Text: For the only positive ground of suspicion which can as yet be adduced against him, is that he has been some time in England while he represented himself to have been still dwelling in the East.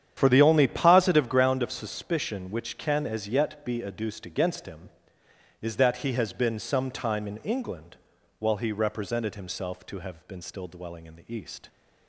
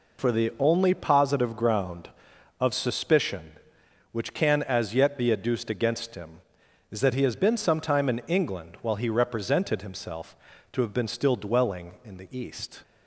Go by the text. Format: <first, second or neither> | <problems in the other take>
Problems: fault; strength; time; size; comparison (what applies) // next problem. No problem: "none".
second | starts louder than the rest; strong; until 1.3 s; 9.5 dB // pauses between "England" and "while"; at 7.9 s; 0.42 s long